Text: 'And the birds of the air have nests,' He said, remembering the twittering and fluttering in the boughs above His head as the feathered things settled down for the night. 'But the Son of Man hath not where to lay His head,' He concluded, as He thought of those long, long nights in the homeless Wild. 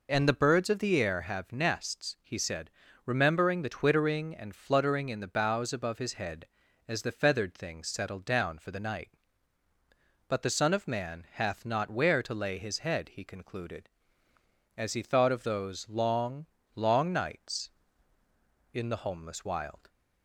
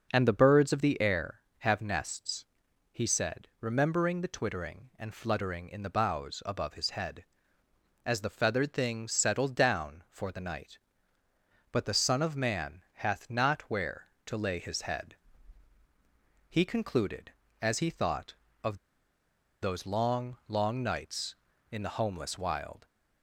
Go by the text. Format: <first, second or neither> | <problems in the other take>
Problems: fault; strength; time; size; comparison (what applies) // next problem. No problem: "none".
first | pauses between "of" and "those"; noticeable; at 18.7 s; 0.84 s long